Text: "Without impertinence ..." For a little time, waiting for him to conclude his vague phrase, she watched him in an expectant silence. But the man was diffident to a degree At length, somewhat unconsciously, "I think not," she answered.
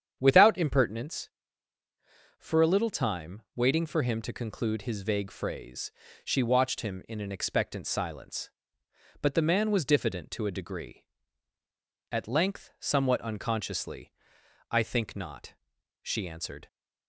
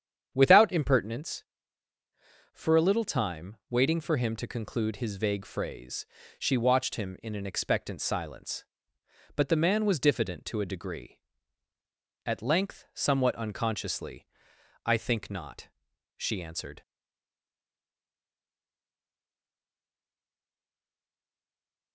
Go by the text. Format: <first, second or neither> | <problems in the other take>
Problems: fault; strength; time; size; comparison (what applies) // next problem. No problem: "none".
first | starts louder than the rest; strong; until 1.3 s; 8.5 dB; strong in the first // stays silent after the last word; strong; from 16.8 s on; 5.1 s long